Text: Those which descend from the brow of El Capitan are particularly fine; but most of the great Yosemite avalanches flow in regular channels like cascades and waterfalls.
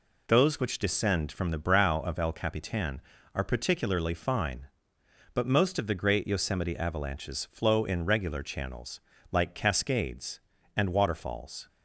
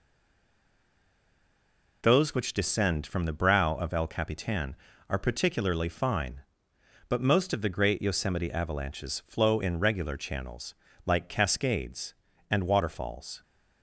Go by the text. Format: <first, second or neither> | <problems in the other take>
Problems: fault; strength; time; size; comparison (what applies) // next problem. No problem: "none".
first | stays silent before the first word; noticeable; until 2.0 s; 2.0 s long // pauses between "channels" and "like"; slight; at 10.7 s; 0.32 s long; slight in the first